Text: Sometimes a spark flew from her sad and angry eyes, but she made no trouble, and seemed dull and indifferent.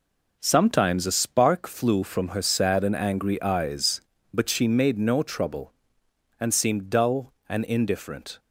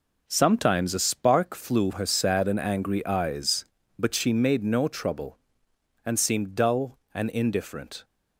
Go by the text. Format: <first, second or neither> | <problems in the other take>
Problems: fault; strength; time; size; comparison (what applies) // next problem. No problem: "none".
first | skips "from"; at 1.9 s